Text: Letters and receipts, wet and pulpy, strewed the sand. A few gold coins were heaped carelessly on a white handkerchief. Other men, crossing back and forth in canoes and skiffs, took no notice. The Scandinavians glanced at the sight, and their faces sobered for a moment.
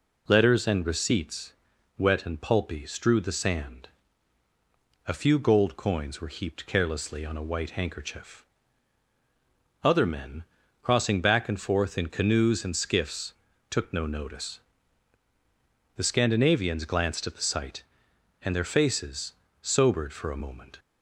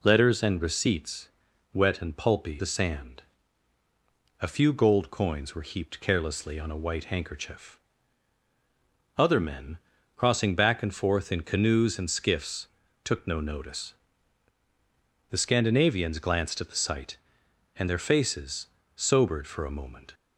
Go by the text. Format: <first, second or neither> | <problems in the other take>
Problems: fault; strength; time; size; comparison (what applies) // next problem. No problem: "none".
first | skips "strewed"; at 2.5 s // pauses between "faces" and "sobered"; slight; at 18.6 s; 0.28 s long; slight in the first